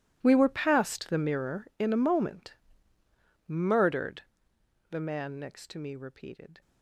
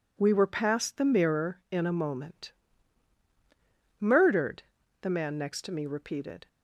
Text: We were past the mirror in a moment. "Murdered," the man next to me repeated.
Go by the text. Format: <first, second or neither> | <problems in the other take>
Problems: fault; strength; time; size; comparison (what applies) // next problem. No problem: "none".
second | gets quieter; strong; throughout; 18.5 dB